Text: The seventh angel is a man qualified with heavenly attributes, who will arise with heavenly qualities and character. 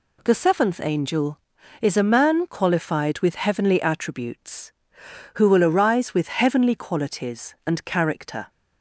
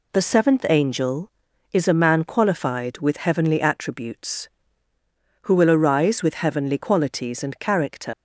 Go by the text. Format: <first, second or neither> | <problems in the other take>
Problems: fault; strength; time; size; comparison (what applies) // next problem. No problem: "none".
first | leaves "character" unfinished; at 8.1 s; 100 ms